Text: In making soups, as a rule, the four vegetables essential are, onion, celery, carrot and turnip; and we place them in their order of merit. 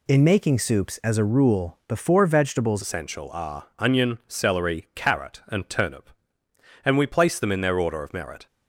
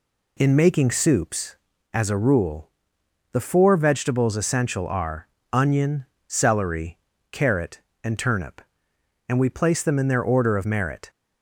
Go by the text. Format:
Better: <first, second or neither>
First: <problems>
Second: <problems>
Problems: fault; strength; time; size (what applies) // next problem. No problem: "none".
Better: second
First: changes voice at "essential"; from 2.8 s on; 5.6 s long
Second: none